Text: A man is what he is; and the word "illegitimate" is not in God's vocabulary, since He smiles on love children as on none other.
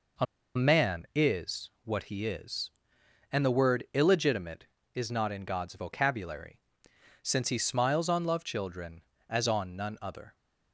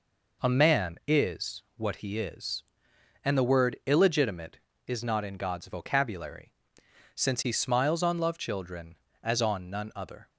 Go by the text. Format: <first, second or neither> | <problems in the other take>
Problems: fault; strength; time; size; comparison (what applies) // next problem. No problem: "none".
second | pauses between "A" and "man"; slight; at 0.2 s; 0.30 s long